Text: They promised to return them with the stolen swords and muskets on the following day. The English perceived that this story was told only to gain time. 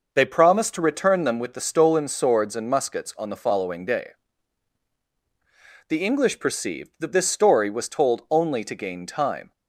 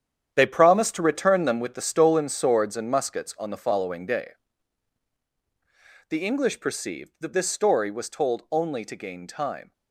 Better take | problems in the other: first | gets quieter; strong; throughout; 11 dB

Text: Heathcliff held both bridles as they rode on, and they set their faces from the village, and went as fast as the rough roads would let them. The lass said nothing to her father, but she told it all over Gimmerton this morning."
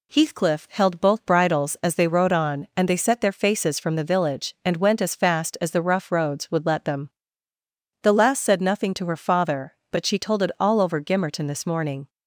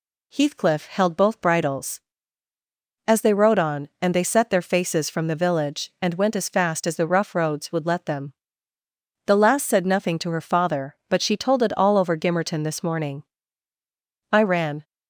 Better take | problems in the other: first | goes on to say "I ran"; from 14.3 s on; 0.54 s long

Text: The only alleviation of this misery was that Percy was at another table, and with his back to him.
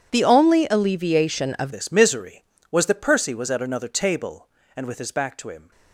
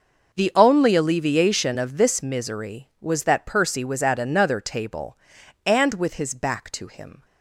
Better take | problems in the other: second | changes voice at "this"; from 1.7 s on; 4.0 s long

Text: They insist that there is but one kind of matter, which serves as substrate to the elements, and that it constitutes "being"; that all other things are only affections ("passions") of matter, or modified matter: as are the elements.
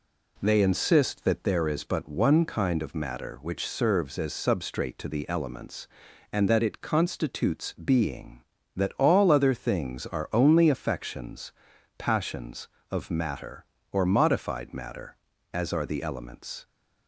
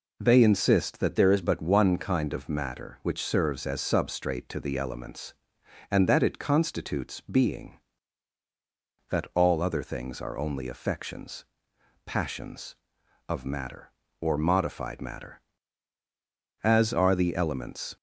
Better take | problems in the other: first | changes voice from "there" to "is"; from 1.1 to 1.4 s; 0.3 s long

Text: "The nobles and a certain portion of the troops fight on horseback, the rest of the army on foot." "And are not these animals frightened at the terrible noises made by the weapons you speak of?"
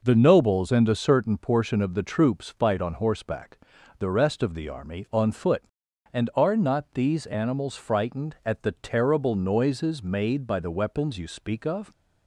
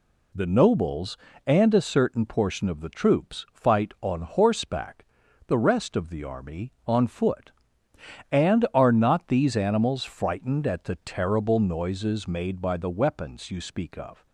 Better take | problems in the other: neither | none

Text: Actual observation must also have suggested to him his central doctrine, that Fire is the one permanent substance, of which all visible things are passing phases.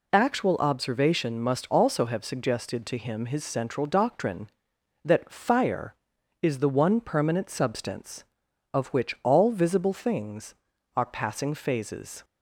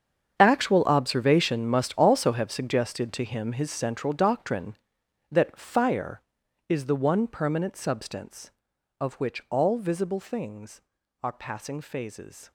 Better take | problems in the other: first | gets quieter; strong; throughout; 15 dB

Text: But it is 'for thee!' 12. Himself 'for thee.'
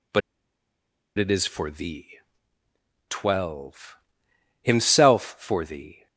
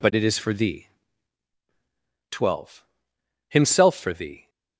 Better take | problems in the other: second | pauses between "But" and "it"; noticeable; at 0.2 s; 0.97 s long

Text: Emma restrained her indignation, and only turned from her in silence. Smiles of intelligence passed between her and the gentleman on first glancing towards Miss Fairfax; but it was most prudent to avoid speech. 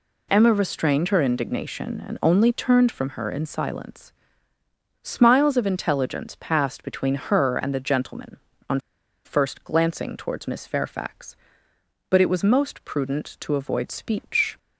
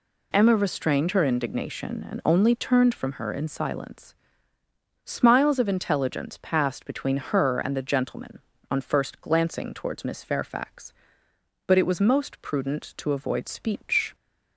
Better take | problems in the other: second | pauses between "on" and "first"; at 8.7 s; 0.45 s long

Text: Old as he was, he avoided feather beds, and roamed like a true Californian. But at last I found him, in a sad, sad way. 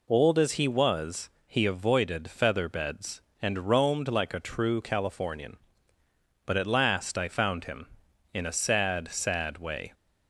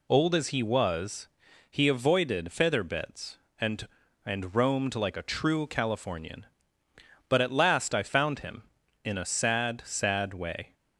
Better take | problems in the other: first | says "and" twice; at 4.2 s

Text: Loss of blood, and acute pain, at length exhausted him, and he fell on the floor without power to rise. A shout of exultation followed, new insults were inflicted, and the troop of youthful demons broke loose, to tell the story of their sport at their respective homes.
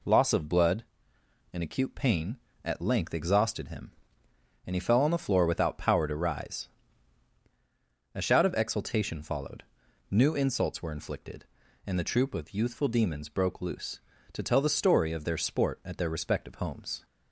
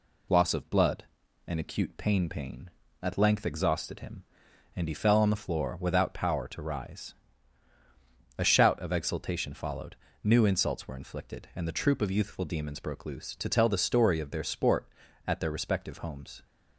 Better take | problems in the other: first | says "pain" twice; at 2.3 s

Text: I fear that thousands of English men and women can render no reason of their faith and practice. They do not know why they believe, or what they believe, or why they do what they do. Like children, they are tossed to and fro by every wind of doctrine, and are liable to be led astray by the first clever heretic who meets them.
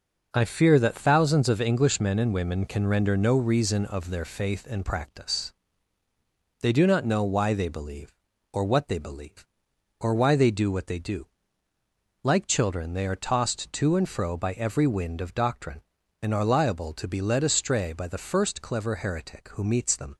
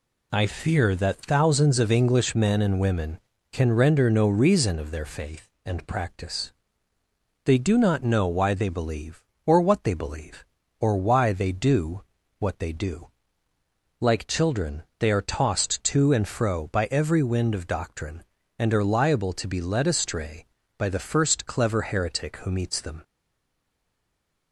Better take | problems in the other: first | pauses between "do" and "what"; slight; at 12.0 s; 0.36 s long // stays silent after the last word; noticeable; from 23.0 s on; 1.5 s long

